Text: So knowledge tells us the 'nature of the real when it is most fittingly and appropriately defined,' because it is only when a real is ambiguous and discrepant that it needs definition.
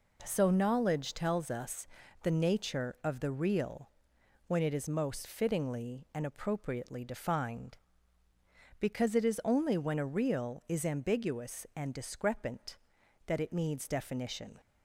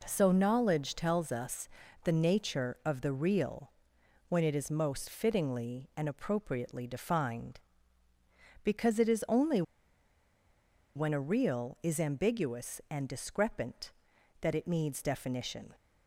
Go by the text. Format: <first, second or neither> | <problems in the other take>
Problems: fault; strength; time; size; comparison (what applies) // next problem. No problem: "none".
first | pauses between "us" and "the"; slight; at 1.6 s; 0.36 s long; slight in the first // pauses between "real" and "when"; noticeable; at 3.7 s; 0.56 s long; noticeable in the first // pauses between "only" and "when"; strong; at 9.5 s; 1.3 s long